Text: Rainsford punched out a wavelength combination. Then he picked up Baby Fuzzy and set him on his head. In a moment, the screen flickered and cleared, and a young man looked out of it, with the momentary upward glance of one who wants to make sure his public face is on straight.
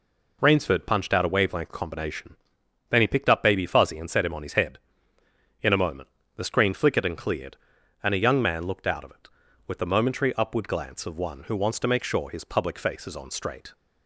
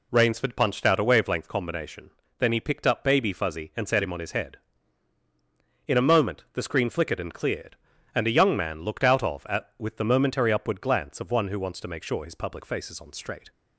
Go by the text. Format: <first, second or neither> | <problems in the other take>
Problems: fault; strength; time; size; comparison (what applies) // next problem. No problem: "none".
first | says "at" for "it"; at 9.4 s